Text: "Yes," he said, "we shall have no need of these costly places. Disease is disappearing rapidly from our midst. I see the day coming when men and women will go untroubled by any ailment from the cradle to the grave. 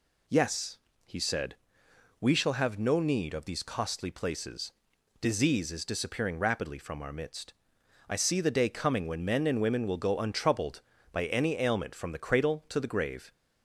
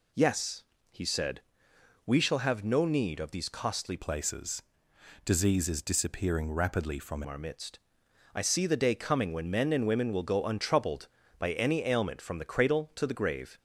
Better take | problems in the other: first | changes voice from "places" to "from"; from 3.9 to 7.2 s; 3.3 s long

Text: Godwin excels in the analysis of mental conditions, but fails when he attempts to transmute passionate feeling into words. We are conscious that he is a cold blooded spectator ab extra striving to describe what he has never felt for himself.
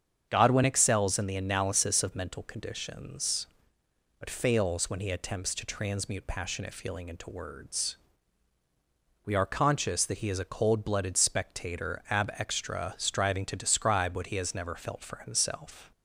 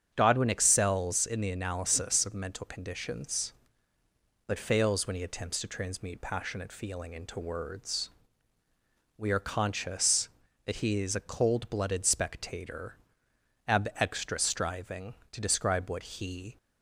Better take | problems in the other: first | starts louder than the rest; strong; until 1.1 s; 7.5 dB; strong in the first // pauses between "spectator" and "ab"; noticeable; at 12.9 s; 0.70 s long // stops before "has never felt for himself"; at 16.5 s

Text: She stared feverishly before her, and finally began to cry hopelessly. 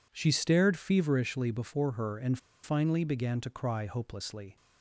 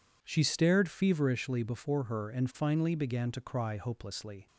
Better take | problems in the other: second | pauses between "and" and "finally"; slight; at 2.3 s; 0.25 s long

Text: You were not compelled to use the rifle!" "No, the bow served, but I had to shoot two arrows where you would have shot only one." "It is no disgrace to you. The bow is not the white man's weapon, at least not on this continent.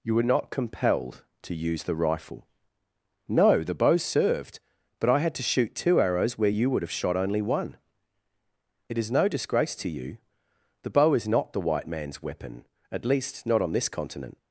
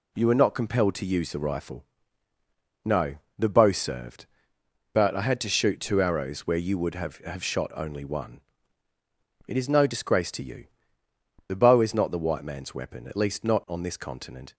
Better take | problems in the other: first | says "have" twice; at 7.2 s

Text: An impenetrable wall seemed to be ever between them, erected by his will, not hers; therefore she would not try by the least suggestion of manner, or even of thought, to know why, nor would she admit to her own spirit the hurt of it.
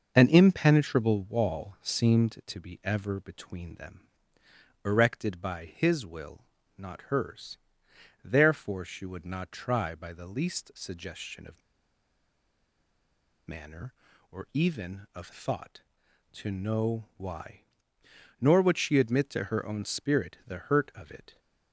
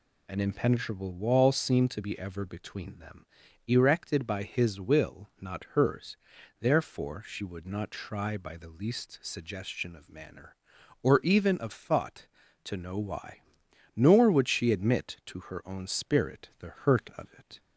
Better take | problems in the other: second | starts louder than the rest; until 1.1 s; 6.5 dB // pauses between "of" and "manner"; strong; at 11.6 s; 1.8 s long

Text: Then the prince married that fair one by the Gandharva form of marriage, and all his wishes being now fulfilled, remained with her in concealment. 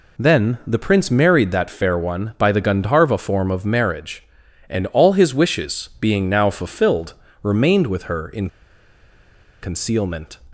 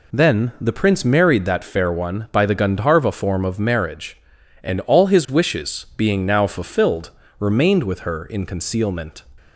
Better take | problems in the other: second | pauses between "in" and "concealment"; at 8.4 s; 1.1 s long

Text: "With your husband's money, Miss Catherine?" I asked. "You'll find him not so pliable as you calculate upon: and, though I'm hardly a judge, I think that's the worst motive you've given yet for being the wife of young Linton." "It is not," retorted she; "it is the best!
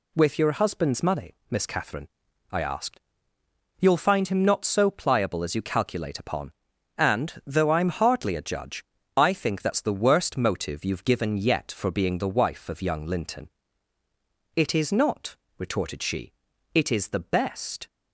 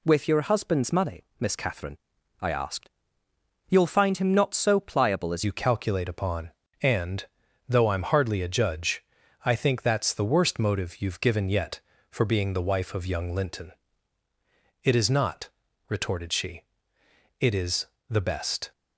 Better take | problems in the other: first | changes voice at "you"; from 5.4 s on; 13.3 s long // pauses between "is" and "the"; slight; at 17.8 s; 0.24 s long

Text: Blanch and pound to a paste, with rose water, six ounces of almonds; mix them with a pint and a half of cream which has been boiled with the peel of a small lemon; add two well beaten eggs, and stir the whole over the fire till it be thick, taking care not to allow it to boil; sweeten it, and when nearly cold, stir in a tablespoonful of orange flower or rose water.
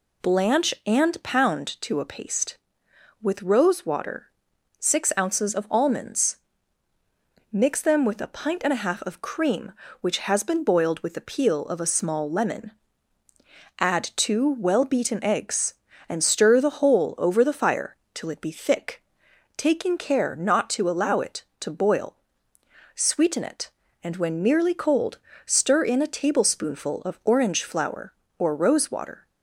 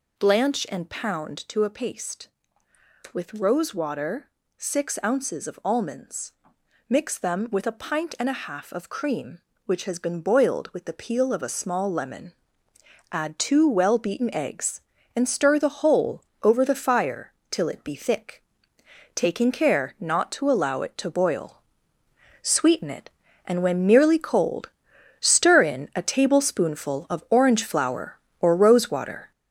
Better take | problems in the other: first | gets louder; noticeable; throughout; 5.5 dB // pauses between "whole" and "over"; slight; at 16.2 s; 0.22 s long // pauses between "fire" and "till"; slight; at 17.3 s; 0.18 s long; slight in the first

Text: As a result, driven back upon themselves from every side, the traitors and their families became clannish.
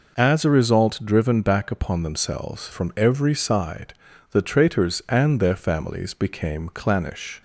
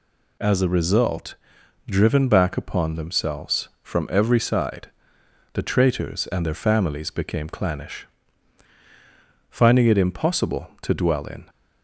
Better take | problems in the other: first | goes on to say "Finding it impossible to dwell in"; strong; from 9.4 s on; 2.0 s long

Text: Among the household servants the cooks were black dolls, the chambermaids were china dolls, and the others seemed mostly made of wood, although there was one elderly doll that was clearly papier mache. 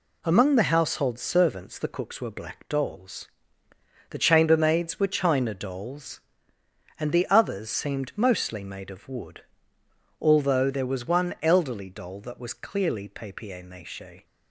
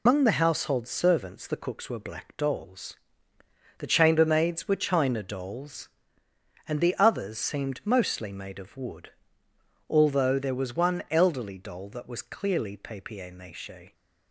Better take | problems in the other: first | loses the start of "Among"; at 0.0 s; 140 ms

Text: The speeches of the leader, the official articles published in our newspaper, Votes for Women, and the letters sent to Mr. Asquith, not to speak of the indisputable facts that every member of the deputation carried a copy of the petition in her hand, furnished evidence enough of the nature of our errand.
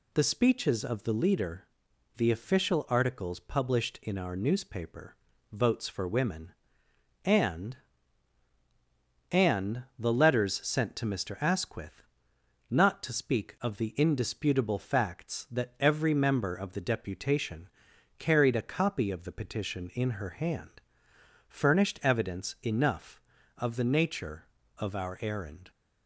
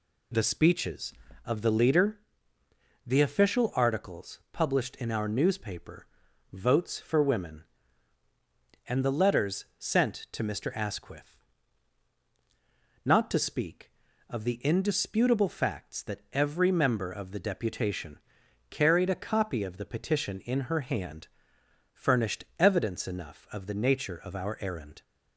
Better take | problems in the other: second | says "and" twice; at 9.2 s // pauses between "deputation" and "carried"; noticeable; at 17.6 s; 0.50 s long; noticeable in the second

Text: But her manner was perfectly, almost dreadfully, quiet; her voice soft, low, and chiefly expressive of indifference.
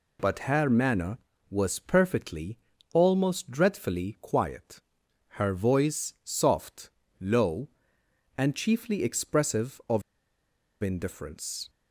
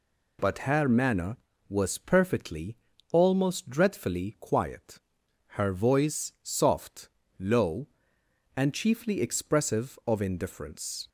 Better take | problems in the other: second | pauses between "of" and "indifference"; noticeable; at 10.0 s; 0.81 s long

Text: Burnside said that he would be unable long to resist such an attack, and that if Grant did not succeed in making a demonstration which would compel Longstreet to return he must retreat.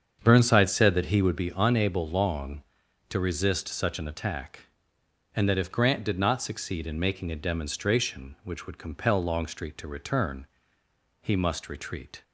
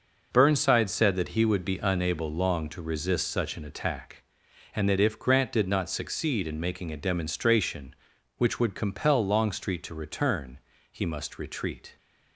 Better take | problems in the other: second | starts louder than the rest; strong; until 1.4 s; 7.5 dB // pauses between "return" and "he"; noticeable; at 10.4 s; 0.76 s long; slight in the second

